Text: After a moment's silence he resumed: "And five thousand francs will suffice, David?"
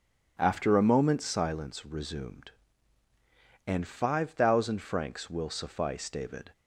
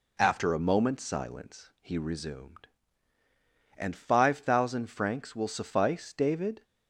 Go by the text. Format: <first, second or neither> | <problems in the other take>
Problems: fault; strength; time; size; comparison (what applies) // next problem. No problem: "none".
second | skips "he"; at 1.8 s